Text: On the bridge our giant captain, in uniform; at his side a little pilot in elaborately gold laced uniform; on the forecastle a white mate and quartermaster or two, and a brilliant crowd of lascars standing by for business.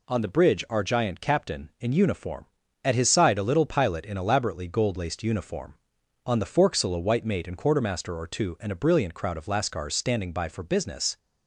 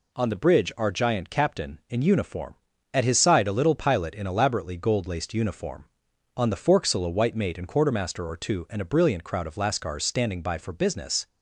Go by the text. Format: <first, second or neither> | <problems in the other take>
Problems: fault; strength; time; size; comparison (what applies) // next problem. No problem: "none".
neither | none